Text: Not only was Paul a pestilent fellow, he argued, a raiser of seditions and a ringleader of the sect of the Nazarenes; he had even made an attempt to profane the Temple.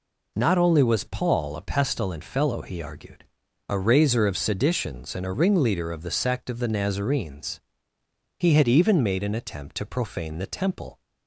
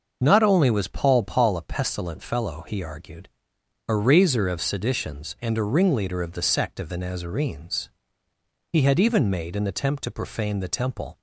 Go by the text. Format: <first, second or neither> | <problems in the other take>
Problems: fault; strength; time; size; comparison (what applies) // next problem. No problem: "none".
first | starts louder than the rest; until 1.2 s; 6.5 dB // says "Paul" twice; at 1.2 s